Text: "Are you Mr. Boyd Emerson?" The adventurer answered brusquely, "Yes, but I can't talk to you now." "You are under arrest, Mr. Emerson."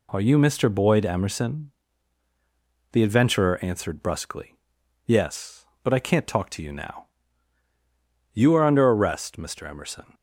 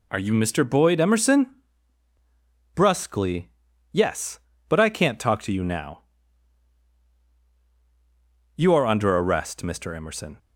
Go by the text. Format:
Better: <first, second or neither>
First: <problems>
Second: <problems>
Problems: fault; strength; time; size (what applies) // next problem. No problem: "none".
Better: first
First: none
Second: skips "The adventurer answered"; at 2.1 s